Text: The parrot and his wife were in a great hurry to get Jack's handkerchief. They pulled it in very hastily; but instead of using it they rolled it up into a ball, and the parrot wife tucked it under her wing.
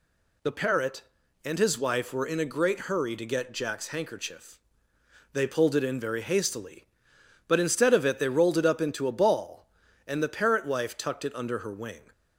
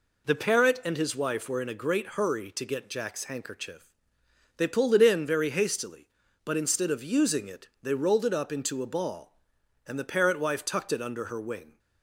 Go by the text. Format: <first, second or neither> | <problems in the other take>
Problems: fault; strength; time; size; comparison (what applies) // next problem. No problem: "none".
second | skips "using"; at 8.0 s